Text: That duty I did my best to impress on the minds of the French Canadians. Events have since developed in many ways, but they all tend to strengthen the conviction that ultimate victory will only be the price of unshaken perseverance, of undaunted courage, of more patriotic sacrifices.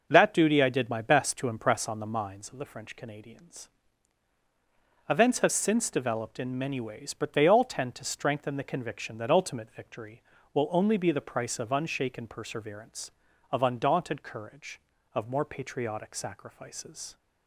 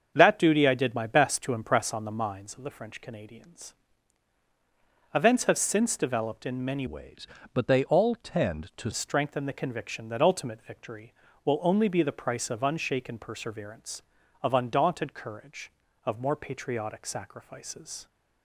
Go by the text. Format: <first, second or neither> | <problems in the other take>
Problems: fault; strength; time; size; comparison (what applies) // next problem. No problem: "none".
first | starts louder than the rest; until 1.1 s; 7 dB // changes voice from "ways" to "to"; from 6.8 to 8.8 s; 2.0 s long